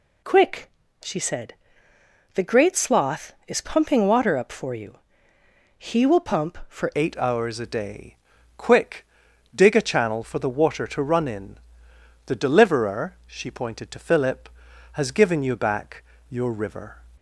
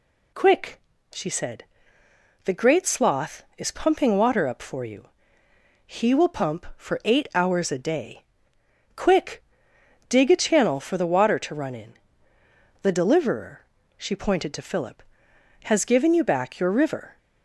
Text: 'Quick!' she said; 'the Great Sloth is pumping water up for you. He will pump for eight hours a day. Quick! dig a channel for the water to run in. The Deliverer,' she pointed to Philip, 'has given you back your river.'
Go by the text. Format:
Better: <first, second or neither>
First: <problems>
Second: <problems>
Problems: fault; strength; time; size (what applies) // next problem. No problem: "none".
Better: second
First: changes voice at "eight"; from 6.9 s on; 10.0 s long // pauses between "back" and "your"; slight; at 16.0 s; 0.24 s long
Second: none